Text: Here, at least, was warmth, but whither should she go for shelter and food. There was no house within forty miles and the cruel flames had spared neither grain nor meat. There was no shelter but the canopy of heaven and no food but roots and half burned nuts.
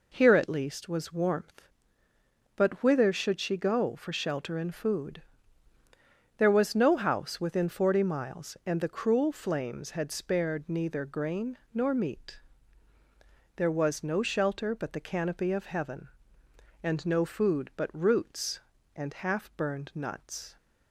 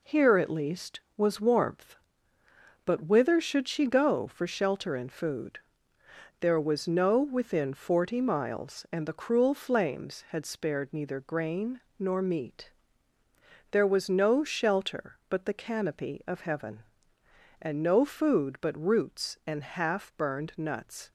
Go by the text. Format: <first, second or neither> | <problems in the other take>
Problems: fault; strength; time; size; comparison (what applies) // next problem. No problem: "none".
first | skips "house"; at 7.2 s // pauses between "grain" and "nor"; slight; at 11.8 s; 0.20 s long; slight in the first